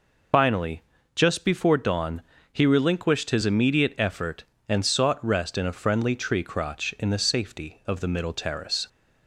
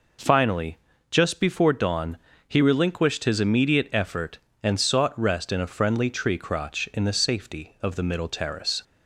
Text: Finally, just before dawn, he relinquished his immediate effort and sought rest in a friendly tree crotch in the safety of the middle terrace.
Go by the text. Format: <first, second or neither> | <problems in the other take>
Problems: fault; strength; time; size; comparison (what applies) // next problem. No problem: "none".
second | loses the start of "Finally"; at 0.3 s; 105 ms